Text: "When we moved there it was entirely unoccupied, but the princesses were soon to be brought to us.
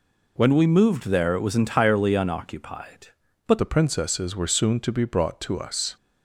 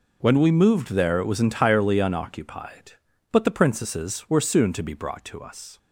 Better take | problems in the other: second | changes voice at "the"; from 3.5 s on; 2.4 s long

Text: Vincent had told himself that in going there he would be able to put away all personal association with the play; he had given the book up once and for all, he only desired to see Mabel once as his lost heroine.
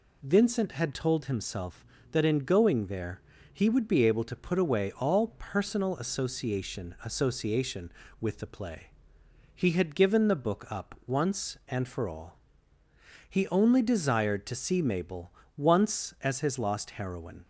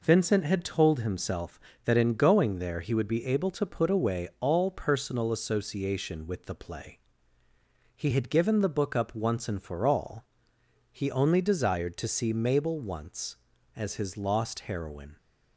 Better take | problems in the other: second | pauses between "there" and "he"; slight; at 3.2 s; 0.32 s long // says "association" twice; at 7.0 s // pauses between "Mabel" and "once"; slight; at 15.3 s; 0.22 s long

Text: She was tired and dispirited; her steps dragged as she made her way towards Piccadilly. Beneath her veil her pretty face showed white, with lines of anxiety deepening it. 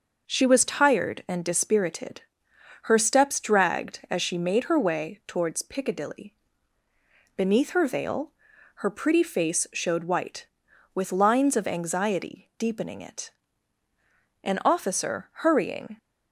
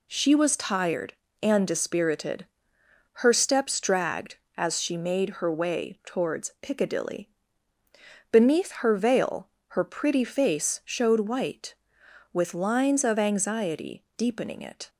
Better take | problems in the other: second | starts louder than the rest; noticeable; until 1.3 s; 6 dB // pauses between "veil" and "her"; noticeable; at 8.3 s; 0.48 s long; slight in the second // goes on to say "An officer hurrying"; from 14.4 s on; 1.5 s long

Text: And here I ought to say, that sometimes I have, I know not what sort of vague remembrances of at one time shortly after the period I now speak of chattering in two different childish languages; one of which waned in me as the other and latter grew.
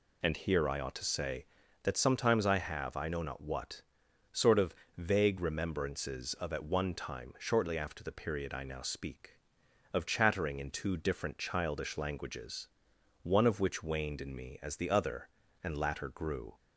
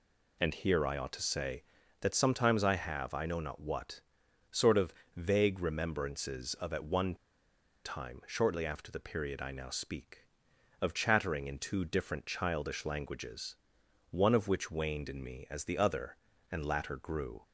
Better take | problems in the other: first | pauses between "what" and "sort"; noticeable; at 4.0 s; 0.52 s long; noticeable in the first // pauses between "of" and "vague"; slight; at 4.9 s; 0.20 s long; slight in the first // pauses between "one" and "time"; noticeable; at 7.1 s; 0.70 s long

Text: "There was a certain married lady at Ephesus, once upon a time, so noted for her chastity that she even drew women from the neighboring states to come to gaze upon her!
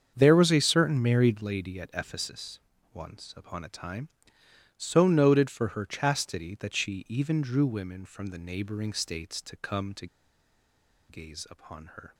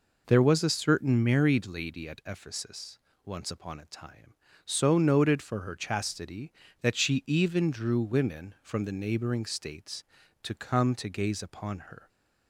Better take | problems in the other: second | starts louder than the rest; strong; until 1.1 s; 7 dB // pauses between "to" and "gaze"; at 10.0 s; 1.0 s long

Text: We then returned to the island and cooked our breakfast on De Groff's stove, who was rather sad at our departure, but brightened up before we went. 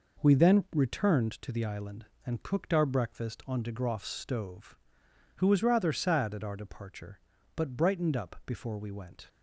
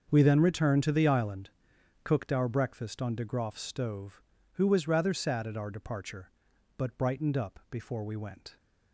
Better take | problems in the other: first | starts louder than the rest; until 1.1 s; 7 dB // skips "and"; at 1.7 s

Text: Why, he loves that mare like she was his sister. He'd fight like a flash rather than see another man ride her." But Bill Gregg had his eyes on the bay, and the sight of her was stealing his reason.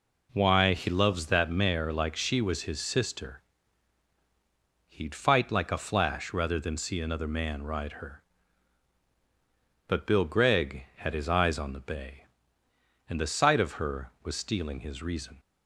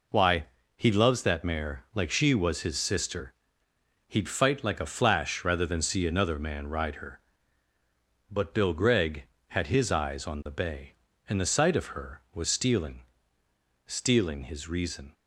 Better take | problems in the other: first | says "stealing" twice; at 13.8 s

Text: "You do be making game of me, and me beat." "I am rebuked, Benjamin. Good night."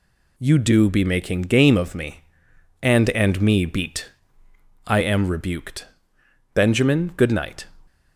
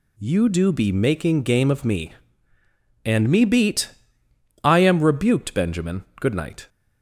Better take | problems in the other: second | says "and" twice; at 3.1 s

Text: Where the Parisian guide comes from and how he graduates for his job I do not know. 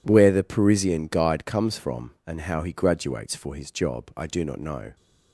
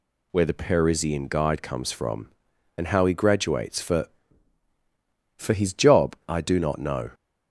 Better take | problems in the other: first | says "for" twice; at 5.3 s

